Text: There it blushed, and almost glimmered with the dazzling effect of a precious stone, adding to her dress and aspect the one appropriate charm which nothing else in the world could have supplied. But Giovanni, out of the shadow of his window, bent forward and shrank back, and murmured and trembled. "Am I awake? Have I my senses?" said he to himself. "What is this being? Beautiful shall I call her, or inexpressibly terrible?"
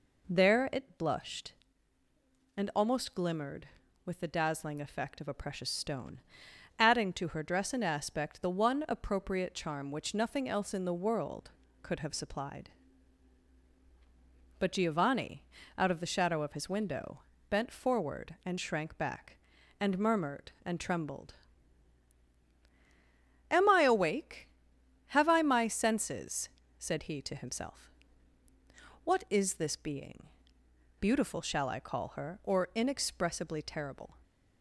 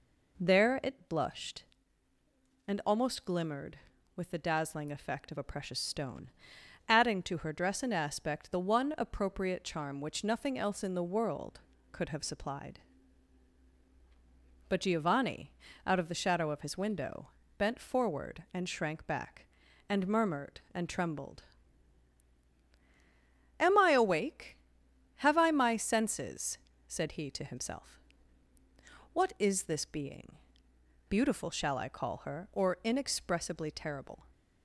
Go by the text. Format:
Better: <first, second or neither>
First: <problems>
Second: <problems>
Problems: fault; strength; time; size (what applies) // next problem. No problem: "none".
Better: neither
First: none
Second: none